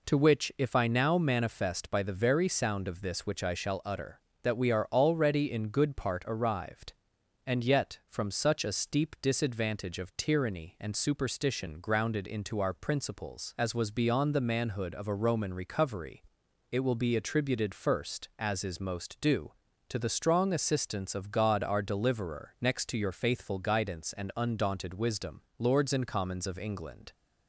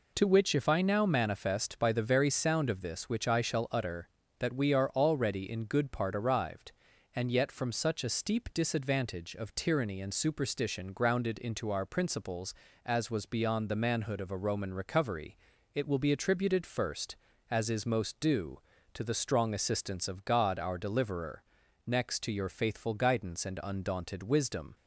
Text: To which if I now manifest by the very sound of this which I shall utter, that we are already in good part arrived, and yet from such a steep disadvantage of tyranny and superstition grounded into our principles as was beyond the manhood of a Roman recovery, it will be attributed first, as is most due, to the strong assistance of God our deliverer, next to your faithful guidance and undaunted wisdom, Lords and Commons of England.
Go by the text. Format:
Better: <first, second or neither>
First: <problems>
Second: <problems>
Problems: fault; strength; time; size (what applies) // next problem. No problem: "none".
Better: first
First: none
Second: stops before "Lords and Commons of England"; at 24.7 s